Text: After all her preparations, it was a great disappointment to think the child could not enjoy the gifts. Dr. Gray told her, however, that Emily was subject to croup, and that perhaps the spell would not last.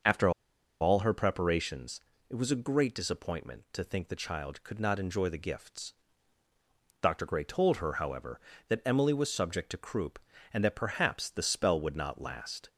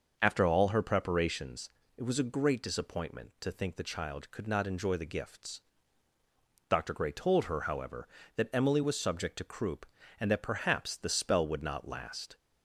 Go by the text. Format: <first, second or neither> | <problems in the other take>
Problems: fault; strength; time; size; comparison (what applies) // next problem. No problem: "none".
second | starts louder than the rest; noticeable; until 1.5 s; 6 dB; noticeable in the second // pauses between "After" and "all"; noticeable; at 0.2 s; 0.51 s long